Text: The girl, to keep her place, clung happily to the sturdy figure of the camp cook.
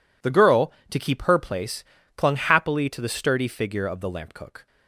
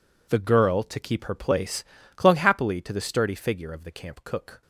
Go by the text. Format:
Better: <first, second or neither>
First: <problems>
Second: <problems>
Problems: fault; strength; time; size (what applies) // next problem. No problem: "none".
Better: second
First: says "lamp" for "camp"; at 4.1 s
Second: none